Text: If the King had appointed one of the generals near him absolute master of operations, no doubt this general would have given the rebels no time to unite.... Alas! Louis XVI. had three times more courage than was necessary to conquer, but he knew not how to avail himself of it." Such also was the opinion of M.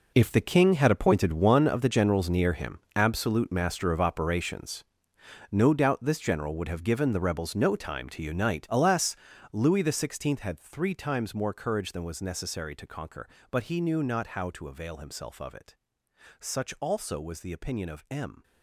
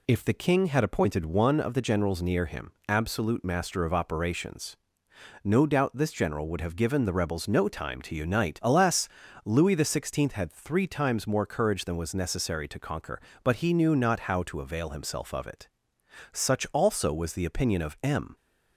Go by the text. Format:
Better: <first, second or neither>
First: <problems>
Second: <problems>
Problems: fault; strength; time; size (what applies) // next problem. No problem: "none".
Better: second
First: gets quieter; strong; throughout; 13.5 dB // pauses between "him" and "absolute"; slight; at 2.7 s; 0.16 s long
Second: pauses between "him" and "absolute"; slight; at 2.7 s; 0.16 s long